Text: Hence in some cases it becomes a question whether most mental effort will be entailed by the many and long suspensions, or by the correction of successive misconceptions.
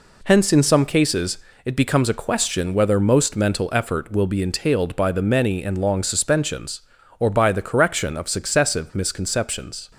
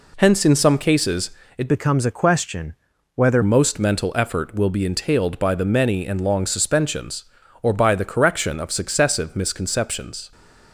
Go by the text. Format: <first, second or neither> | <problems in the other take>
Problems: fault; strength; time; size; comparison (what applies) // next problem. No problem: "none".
first | pauses between "cases" and "it"; slight; at 1.3 s; 0.26 s long; slight in the first // changes voice from "becomes" to "whether"; from 1.6 to 3.4 s; 1.8 s long // pauses between "question" and "whether"; at 2.7 s; 0.42 s long